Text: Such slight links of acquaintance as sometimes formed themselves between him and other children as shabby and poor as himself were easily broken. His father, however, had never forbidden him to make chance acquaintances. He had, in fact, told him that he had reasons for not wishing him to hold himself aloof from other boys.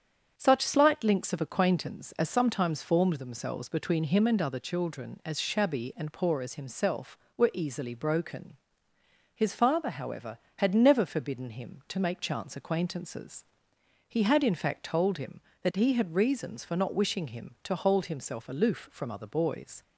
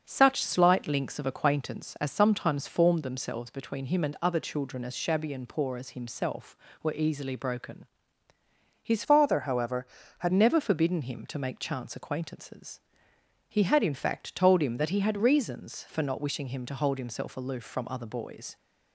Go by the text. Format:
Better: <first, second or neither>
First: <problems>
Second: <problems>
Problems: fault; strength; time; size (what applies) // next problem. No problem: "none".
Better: first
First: starts louder than the rest; strong; until 1.3 s; 8 dB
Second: starts louder than the rest; until 1.0 s; 6.5 dB // changes voice from "father" to "had"; from 9.0 to 10.3 s; 1.3 s long